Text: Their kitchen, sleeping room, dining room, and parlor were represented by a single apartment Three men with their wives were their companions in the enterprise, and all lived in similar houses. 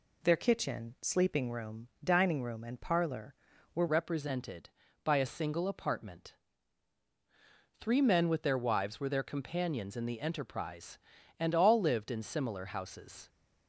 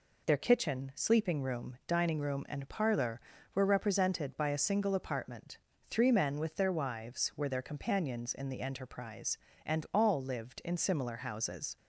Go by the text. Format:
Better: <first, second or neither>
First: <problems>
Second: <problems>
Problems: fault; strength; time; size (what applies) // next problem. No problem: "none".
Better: second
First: changes voice at "represented"; from 3.8 s on; 9.4 s long // pauses between "apartment" and "Three"; strong; at 6.3 s; 1.4 s long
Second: pauses between "apartment" and "Three"; slight; at 5.5 s; 0.34 s long